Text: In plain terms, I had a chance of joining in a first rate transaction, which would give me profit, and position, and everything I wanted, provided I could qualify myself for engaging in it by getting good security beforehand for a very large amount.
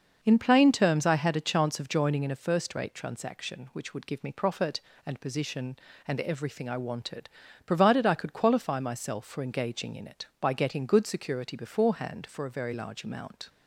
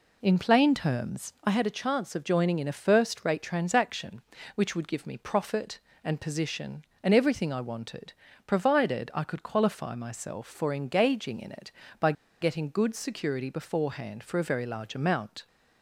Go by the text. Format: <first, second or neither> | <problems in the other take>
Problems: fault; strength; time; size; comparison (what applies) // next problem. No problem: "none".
first | pauses between "by" and "getting"; slight; at 12.1 s; 0.28 s long